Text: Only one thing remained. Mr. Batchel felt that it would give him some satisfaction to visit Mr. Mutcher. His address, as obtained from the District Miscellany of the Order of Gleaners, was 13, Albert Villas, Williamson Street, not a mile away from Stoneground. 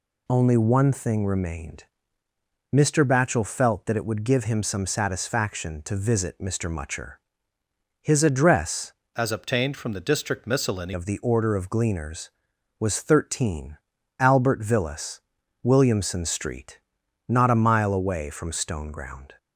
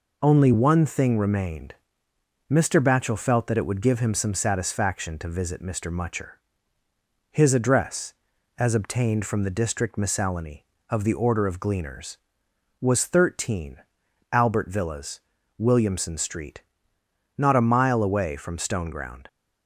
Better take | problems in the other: second | changes voice from "as" to "Miscellany"; from 9.1 to 10.9 s; 1.8 s long

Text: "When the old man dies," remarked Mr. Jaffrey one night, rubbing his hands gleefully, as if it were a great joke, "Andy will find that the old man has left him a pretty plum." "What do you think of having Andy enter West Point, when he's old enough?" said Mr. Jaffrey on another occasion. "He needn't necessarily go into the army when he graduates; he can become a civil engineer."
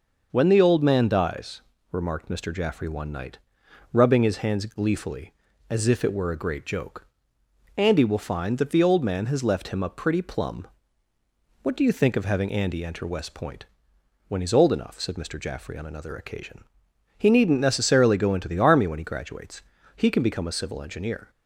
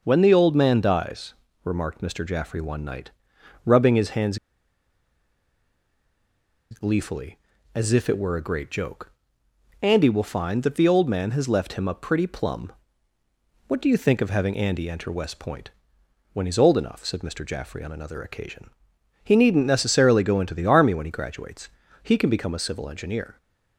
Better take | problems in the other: first | pauses between "hands" and "gleefully"; strong; at 4.3 s; 2.3 s long

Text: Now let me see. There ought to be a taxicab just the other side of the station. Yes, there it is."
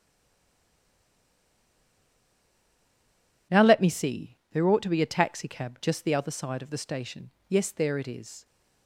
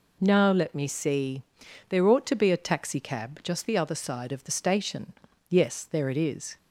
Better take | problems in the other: second | stays silent before the first word; strong; until 3.5 s; 3.5 s long

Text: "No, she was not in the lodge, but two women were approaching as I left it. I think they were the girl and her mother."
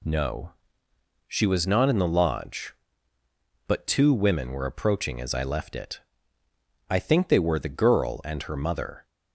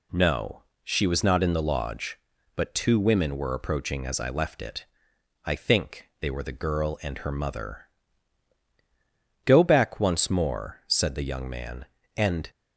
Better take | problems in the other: first | goes on to say "Go back once more said the young man and"; strong; from 9.4 s on; 3.0 s long

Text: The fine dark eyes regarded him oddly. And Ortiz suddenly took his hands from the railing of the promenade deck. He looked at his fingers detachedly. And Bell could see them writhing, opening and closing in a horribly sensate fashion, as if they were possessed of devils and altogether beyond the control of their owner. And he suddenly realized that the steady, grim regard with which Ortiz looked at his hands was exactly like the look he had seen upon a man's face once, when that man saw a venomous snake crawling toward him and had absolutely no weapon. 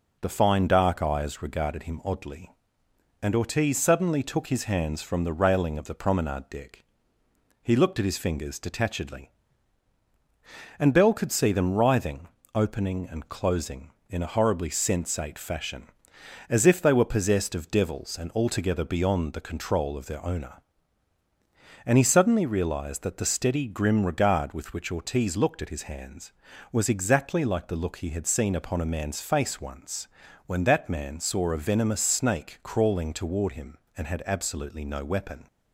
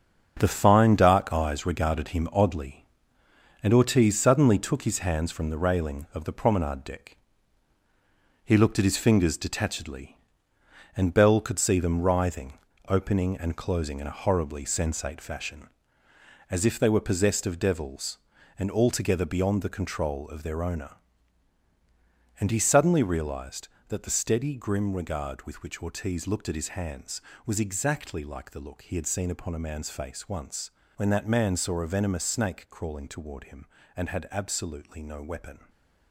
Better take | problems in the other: first | gets quieter; strong; throughout; 9 dB

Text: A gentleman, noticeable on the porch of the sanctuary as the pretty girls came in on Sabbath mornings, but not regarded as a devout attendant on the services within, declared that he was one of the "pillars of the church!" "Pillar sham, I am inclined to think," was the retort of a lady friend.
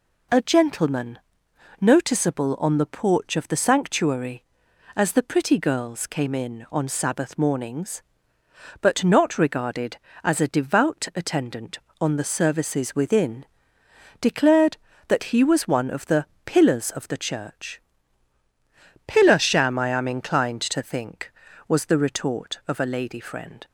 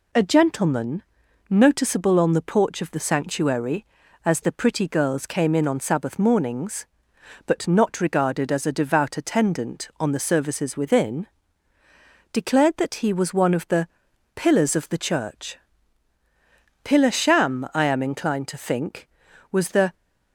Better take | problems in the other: first | pauses between "the" and "pillars"; noticeable; at 13.8 s; 0.48 s long; slight in the first // stops before "retort of a lady friend"; at 19.9 s

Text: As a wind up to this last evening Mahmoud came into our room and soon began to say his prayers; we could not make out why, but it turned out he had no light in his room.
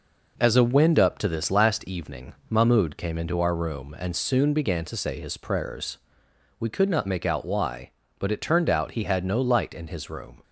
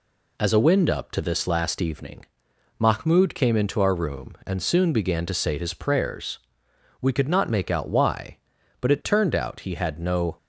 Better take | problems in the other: first | pauses between "evening" and "Mahmoud"; noticeable; at 2.2 s; 0.52 s long // stops before "light in his room"; at 10.3 s

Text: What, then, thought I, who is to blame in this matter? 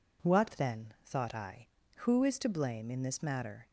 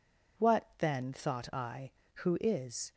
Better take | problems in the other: first | stops before "to blame in this matter"; at 2.9 s

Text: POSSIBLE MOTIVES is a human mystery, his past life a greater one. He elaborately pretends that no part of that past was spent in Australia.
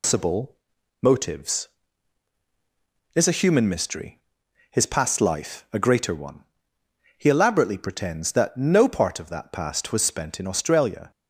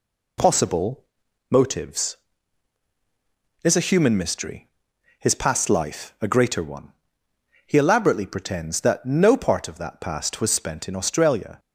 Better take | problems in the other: second | loses the start of "POSSIBLE"; at 0.0 s; 145 ms // pauses between "POSSIBLE" and "MOTIVES"; noticeable; at 0.5 s; 0.48 s long; noticeable in the second

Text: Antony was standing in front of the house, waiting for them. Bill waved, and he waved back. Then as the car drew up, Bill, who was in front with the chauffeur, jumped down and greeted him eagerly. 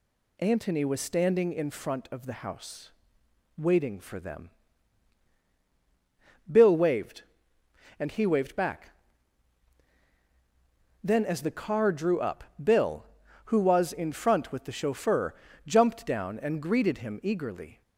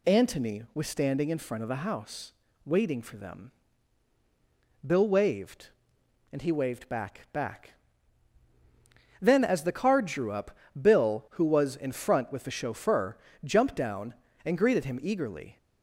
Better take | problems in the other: first | says "back" twice; at 7.3 s

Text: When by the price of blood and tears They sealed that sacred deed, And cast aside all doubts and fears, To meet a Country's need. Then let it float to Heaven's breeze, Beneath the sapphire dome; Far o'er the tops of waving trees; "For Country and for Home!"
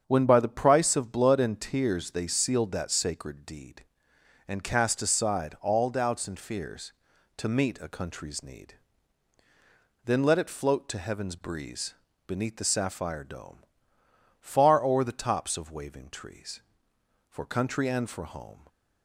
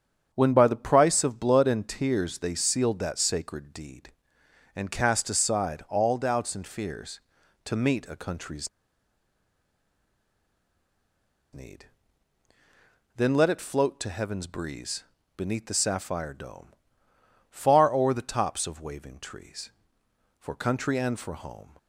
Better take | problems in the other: first | starts louder than the rest; strong; until 1.3 s; 7.5 dB; strong in the first // pauses between "Country's" and "need"; strong; at 8.6 s; 2.8 s long

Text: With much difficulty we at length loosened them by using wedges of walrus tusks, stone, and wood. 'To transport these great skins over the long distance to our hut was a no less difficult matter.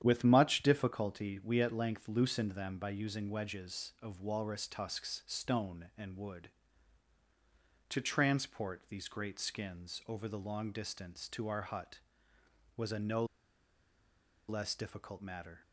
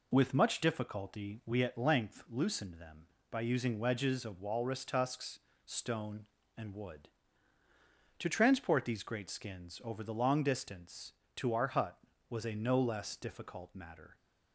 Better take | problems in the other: second | starts louder than the rest; strong; until 1.0 s; 9.5 dB // pauses between "no" and "less"; at 13.2 s; 1.2 s long

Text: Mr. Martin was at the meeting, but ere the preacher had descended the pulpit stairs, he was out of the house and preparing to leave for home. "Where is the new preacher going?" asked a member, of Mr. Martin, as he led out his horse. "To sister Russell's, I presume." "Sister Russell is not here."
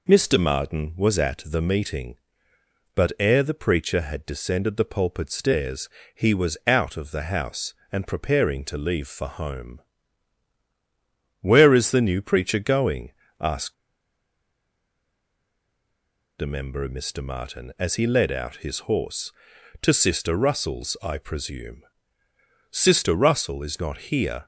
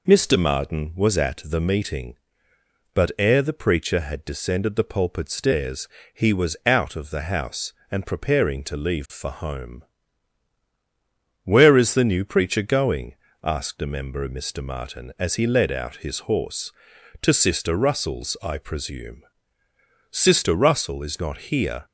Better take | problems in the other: second | pauses between "asked" and "a"; strong; at 13.7 s; 2.6 s long

